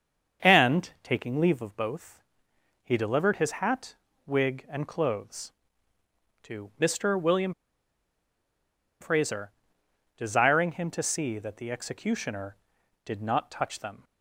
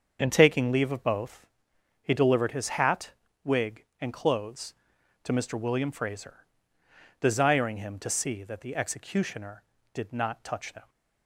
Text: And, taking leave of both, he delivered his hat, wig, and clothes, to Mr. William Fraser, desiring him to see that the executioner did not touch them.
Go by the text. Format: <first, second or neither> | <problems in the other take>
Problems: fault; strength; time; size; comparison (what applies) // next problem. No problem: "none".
second | starts louder than the rest; until 1.5 s; 7 dB; also in the second // pauses between "William" and "Fraser"; strong; at 7.5 s; 1.4 s long